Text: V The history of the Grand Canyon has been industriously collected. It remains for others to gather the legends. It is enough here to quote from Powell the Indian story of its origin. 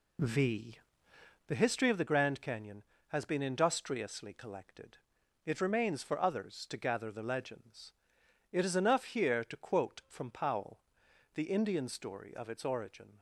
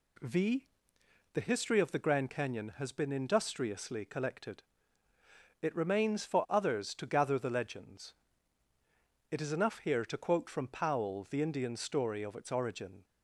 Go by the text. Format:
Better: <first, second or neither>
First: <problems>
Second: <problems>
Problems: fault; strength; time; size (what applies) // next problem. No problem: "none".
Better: second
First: starts louder than the rest; slight; until 1.5 s; 2 dB // pauses between "V" and "The"; noticeable; at 0.7 s; 0.70 s long // pauses between "Powell" and "the"; noticeable; at 10.8 s; 0.54 s long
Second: pauses between "V" and "The"; noticeable; at 0.6 s; 0.68 s long